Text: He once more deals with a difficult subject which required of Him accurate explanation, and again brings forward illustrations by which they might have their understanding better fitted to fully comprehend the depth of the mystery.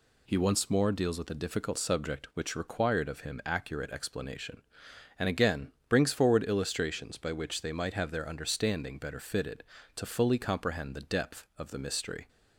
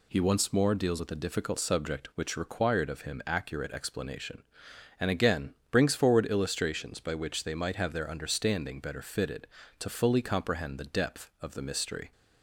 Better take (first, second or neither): neither